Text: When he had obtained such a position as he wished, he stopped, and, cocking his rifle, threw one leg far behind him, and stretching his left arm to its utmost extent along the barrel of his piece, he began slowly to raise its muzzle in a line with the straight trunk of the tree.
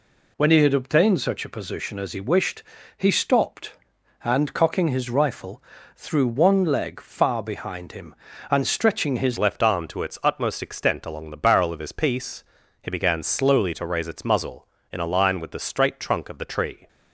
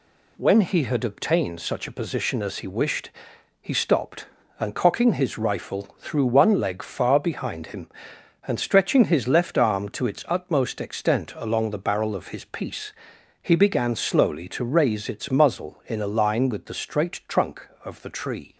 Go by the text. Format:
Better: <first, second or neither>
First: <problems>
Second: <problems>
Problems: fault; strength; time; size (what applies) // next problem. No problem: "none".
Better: second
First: changes voice at "left"; from 9.3 s on; 7.5 s long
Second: none